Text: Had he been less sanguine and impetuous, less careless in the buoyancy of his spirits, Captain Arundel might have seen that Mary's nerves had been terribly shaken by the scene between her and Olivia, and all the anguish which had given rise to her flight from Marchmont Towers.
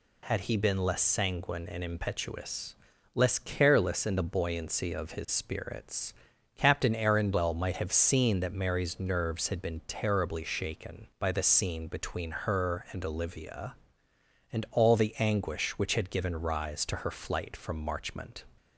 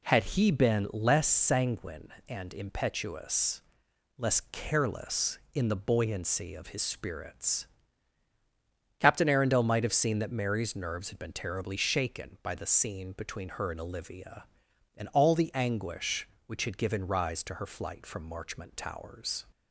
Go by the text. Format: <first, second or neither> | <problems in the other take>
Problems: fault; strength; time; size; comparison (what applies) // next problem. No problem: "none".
second | stops before "Towers"; at 18.5 s